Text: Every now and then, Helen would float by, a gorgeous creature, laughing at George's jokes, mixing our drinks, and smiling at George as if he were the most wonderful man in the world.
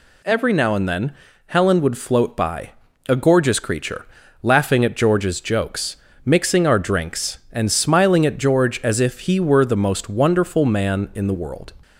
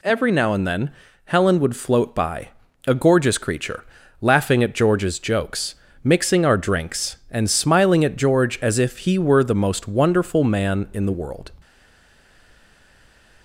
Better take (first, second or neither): first